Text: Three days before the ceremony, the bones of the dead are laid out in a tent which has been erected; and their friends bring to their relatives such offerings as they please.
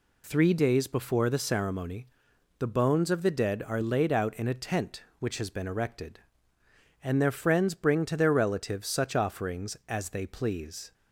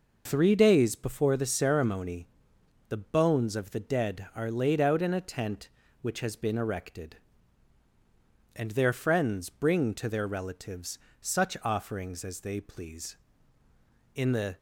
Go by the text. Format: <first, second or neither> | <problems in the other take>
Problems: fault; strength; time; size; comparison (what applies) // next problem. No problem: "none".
first | pauses between "relatives" and "such"; slight; at 10.9 s; 0.24 s long // goes on to say "In the"; slight; from 14.1 s on; 0.42 s long